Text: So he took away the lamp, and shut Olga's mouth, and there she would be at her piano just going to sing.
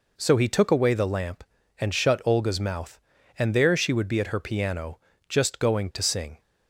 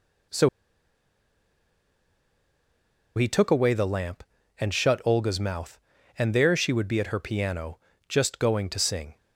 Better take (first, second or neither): first